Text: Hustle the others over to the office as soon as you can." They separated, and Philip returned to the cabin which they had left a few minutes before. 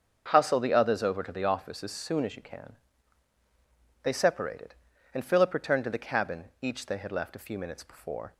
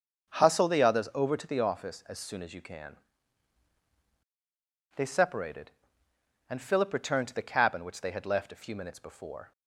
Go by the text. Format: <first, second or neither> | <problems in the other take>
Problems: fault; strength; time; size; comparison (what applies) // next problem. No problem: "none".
second | starts louder than the rest; until 1.3 s; 6.5 dB; also in the second // says "each" for "which"; at 6.6 s